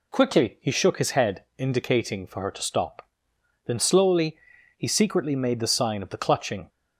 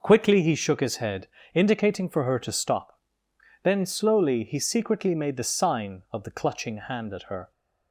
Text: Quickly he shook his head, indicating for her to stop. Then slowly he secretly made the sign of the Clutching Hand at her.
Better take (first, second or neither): second